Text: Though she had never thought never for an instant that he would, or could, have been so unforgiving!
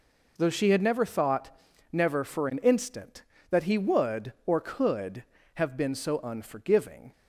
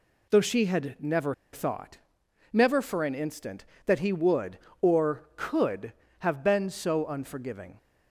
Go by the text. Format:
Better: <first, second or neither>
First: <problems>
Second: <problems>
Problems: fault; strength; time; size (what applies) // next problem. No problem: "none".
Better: first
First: pauses between "thought" and "never"; at 1.5 s; 0.40 s long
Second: pauses between "never" and "thought"; slight; at 1.3 s; 0.19 s long // pauses between "thought" and "never"; noticeable; at 1.9 s; 0.54 s long